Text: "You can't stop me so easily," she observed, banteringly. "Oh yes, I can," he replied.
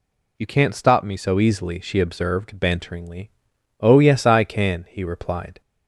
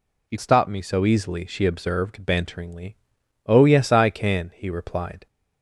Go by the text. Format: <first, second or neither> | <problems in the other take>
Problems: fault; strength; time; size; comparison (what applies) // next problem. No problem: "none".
first | skips "can't"; at 0.3 s